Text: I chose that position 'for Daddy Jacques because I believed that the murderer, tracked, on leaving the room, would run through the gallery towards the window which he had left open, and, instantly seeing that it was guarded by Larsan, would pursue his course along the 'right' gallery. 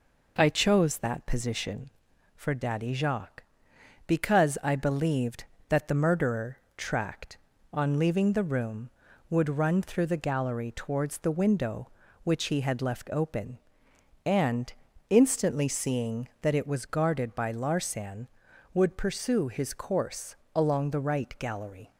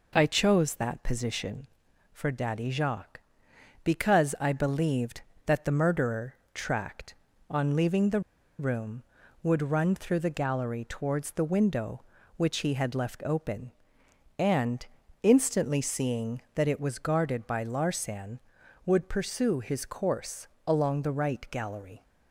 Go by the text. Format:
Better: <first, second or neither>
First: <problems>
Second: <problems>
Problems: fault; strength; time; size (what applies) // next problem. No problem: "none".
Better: first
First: pauses between "course" and "along"; slight; at 20.3 s; 0.18 s long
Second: pauses between "the" and "room"; at 8.1 s; 0.39 s long // pauses between "course" and "along"; slight; at 20.4 s; 0.18 s long